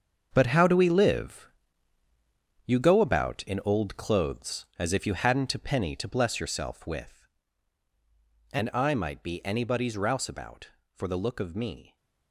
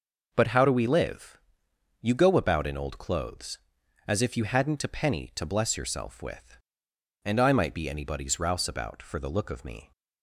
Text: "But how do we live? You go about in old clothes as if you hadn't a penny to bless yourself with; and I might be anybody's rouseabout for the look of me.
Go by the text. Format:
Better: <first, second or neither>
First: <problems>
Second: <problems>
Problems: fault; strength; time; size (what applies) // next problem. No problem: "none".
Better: second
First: gets quieter; strong; throughout; 11 dB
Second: none